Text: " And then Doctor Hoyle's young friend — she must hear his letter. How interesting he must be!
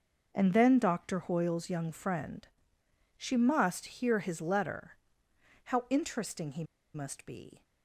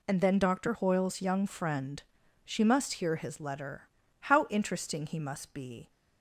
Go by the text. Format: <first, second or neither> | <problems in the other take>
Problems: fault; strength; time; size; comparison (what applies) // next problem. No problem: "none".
second | pauses between "he" and "must"; slight; at 6.6 s; 0.29 s long